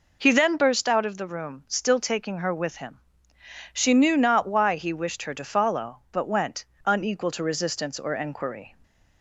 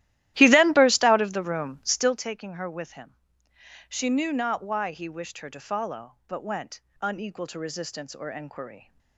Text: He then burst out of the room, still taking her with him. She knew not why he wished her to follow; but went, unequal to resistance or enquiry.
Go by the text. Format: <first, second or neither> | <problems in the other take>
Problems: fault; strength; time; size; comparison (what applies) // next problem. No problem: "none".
first | starts louder than the rest; strong; until 2.2 s; 14.5 dB